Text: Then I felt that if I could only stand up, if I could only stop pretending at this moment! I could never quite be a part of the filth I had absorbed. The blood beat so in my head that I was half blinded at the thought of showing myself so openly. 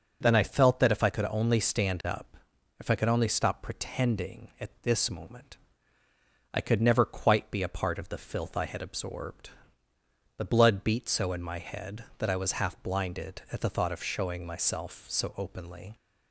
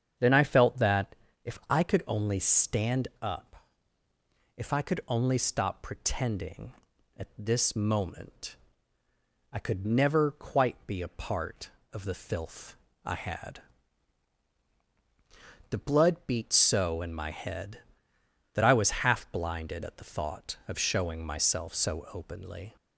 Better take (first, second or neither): first